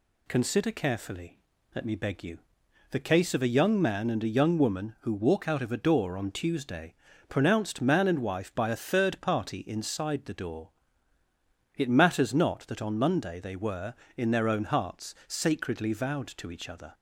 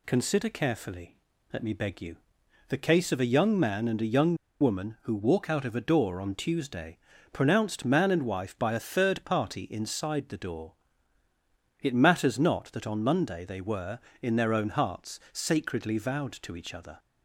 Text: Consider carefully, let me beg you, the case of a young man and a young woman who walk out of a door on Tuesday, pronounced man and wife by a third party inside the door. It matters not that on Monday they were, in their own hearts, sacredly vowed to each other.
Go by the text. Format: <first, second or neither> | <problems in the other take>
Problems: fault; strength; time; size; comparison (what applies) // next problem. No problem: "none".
first | pauses between "young" and "woman"; slight; at 4.3 s; 0.24 s long